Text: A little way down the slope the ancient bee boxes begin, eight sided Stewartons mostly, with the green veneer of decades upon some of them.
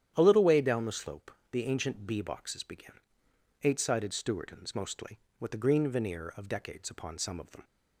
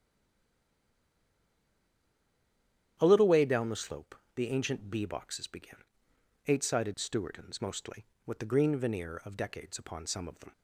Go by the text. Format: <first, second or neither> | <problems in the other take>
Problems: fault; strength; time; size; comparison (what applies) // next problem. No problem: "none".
first | stays silent before the first word; strong; until 2.9 s; 2.9 s long // starts louder than the rest; strong; until 4.0 s; 10.5 dB; strong in the first // pauses between "slope" and "the"; slight; at 4.1 s; 0.18 s long; slight in the first